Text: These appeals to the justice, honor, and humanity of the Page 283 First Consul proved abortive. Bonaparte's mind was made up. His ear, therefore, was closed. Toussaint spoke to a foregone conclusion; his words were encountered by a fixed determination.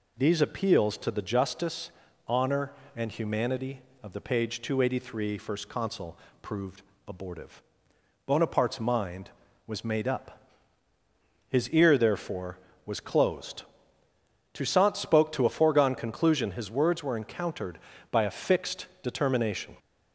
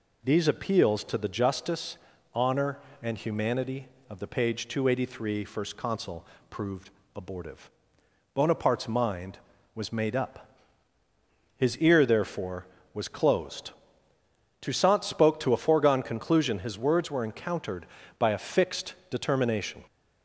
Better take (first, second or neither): neither